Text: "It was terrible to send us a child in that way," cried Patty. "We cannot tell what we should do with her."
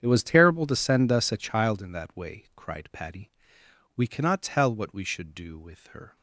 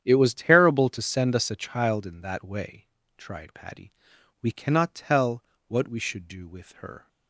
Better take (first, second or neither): first